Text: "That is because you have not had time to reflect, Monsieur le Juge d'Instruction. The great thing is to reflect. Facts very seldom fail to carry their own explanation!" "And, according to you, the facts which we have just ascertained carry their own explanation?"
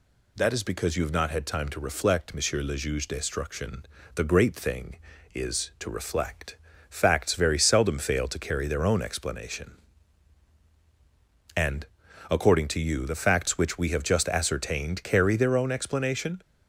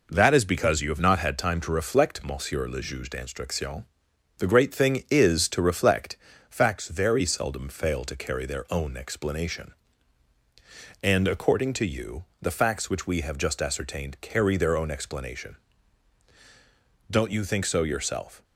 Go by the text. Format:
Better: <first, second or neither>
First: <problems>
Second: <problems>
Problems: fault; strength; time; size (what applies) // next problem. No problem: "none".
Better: first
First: none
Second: goes on to say "Don't you think so yourself"; from 17.0 s on; 1.3 s long